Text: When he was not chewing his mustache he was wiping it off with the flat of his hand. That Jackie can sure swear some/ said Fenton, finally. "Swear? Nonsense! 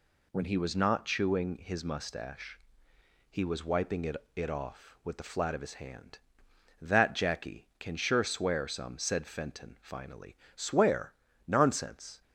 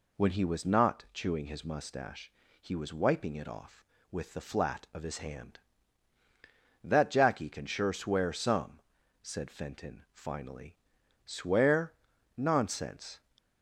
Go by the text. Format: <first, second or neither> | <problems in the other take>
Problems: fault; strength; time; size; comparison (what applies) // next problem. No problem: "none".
second | pauses between "mustache" and "he"; noticeable; at 2.5 s; 0.72 s long; slight in the second // says "it" twice; at 4.3 s